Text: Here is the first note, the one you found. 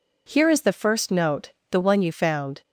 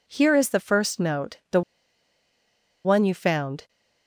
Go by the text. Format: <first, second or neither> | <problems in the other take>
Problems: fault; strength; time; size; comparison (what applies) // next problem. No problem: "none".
first | pauses between "the" and "one"; at 1.6 s; 1.2 s long